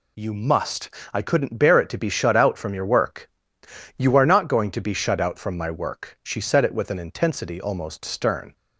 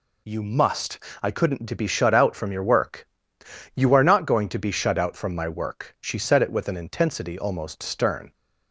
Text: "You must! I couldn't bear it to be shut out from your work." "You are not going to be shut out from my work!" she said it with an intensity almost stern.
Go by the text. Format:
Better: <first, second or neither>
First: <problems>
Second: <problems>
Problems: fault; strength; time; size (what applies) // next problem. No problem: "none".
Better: first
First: none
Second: skips "bear it"; at 1.6 s